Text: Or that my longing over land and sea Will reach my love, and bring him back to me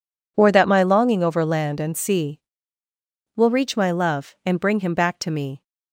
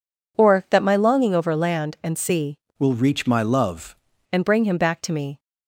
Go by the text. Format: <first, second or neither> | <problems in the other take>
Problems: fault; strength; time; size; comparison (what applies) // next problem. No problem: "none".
first | changes voice from "Will" to "love"; from 2.7 to 3.9 s; 1.2 s long